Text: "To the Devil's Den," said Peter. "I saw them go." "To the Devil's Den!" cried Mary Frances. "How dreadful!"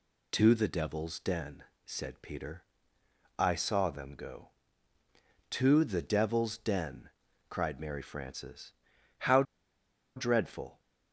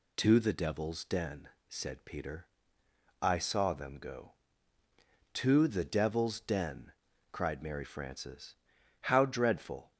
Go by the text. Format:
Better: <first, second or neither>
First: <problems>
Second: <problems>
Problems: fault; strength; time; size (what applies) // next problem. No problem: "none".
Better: second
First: pauses between "How" and "dreadful"; noticeable; at 9.4 s; 0.73 s long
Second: none